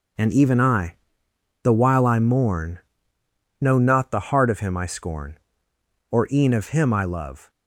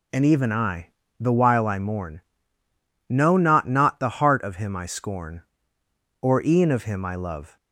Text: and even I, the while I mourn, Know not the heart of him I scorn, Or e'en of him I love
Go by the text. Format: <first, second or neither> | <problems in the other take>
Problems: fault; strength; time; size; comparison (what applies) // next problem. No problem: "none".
first | says "not" twice; at 3.6 s